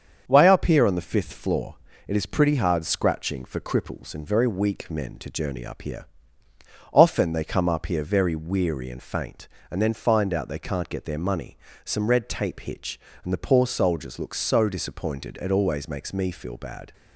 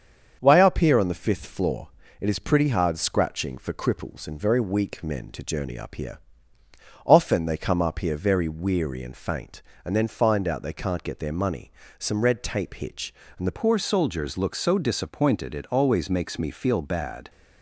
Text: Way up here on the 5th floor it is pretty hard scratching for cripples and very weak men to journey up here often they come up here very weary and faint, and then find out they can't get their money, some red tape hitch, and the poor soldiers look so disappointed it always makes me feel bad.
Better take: first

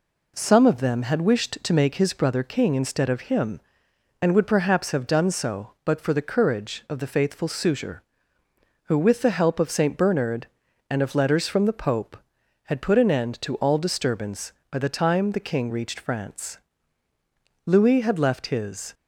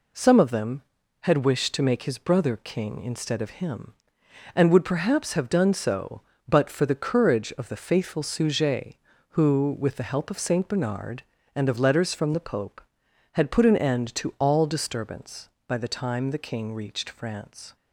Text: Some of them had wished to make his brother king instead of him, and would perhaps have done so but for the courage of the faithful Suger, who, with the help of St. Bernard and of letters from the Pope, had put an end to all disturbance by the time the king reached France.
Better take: second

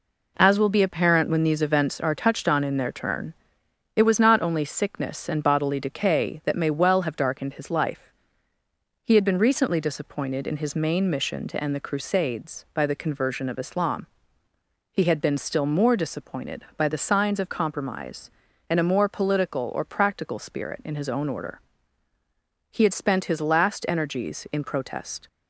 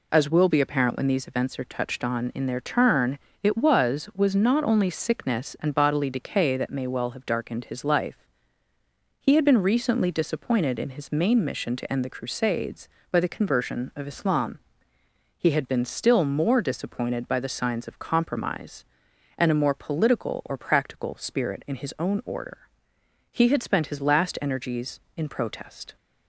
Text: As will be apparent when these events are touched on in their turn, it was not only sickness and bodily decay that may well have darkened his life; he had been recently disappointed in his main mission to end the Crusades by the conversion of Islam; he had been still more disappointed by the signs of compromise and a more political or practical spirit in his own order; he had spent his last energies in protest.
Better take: first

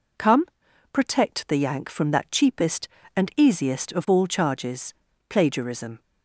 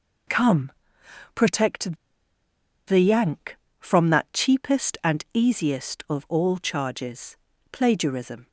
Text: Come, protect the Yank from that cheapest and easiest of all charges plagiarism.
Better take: first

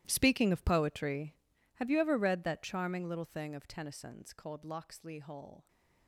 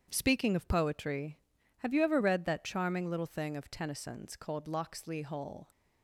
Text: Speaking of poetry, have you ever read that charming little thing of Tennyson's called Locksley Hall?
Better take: second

